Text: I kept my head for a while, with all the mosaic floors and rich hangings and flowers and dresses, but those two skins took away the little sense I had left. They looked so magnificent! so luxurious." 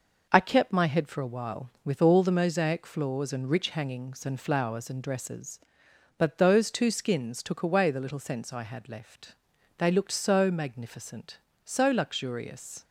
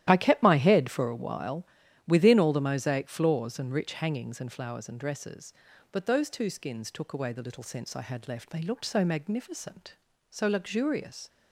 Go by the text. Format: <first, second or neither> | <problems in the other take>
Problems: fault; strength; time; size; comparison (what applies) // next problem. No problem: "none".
first | starts louder than the rest; strong; until 1.1 s; 12.5 dB // says "within" for "with"; at 2.0 s